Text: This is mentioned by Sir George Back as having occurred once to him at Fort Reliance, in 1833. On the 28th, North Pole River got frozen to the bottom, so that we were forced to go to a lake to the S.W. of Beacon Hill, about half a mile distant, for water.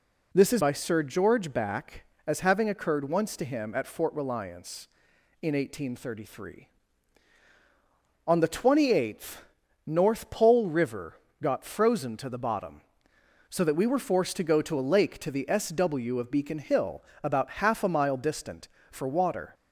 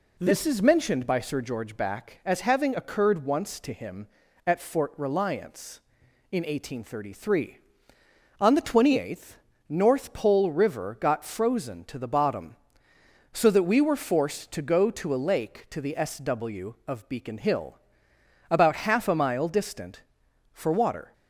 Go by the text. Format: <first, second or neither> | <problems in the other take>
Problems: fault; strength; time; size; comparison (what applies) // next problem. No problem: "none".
second | skips "mentioned"; at 0.6 s // pauses between "River" and "got"; slight; at 11.1 s; 0.20 s long